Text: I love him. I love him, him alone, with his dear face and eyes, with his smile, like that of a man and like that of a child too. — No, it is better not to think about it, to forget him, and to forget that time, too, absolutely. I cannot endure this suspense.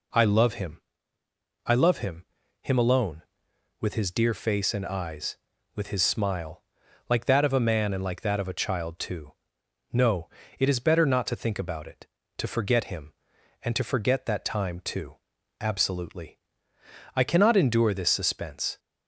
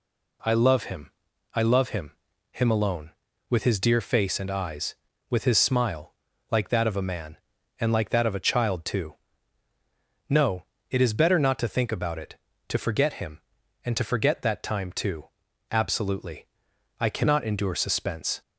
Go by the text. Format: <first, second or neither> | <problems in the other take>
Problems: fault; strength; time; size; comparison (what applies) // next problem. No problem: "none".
first | skips "this"; at 17.7 s